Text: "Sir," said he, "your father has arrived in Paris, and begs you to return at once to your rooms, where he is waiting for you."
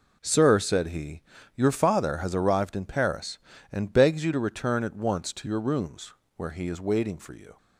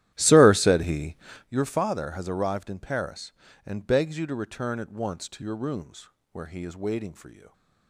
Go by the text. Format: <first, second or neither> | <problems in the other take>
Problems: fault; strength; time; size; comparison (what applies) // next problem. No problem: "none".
first | starts louder than the rest; strong; until 1.5 s; 13 dB